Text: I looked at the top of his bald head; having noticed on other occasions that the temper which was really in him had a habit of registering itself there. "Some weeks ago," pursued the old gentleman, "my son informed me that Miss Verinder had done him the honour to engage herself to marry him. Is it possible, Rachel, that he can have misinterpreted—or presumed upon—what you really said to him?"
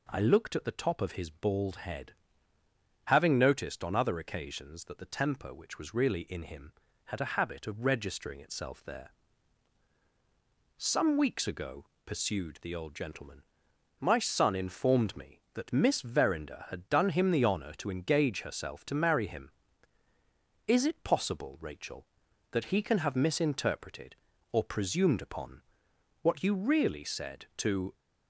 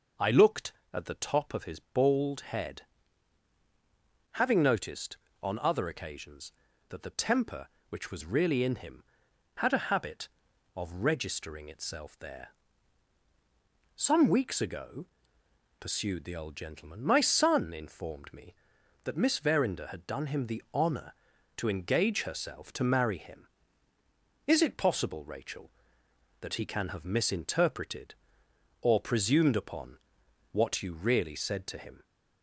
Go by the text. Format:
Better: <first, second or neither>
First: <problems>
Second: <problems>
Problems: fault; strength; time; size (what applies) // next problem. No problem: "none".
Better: second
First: stops before "him"; at 27.9 s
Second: none